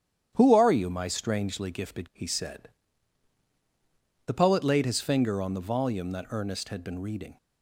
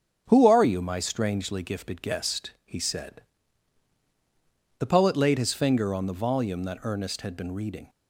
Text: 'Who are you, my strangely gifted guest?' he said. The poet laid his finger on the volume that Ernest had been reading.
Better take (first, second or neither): second